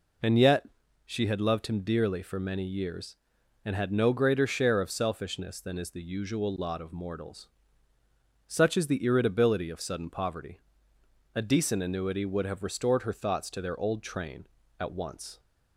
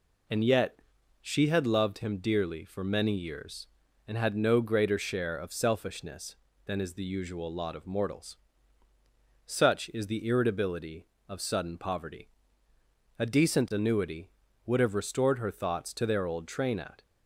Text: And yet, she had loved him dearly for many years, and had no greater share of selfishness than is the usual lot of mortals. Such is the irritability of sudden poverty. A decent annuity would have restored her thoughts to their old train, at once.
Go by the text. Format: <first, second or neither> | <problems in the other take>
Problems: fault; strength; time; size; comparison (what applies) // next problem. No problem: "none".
first | stops before "once"; at 17.0 s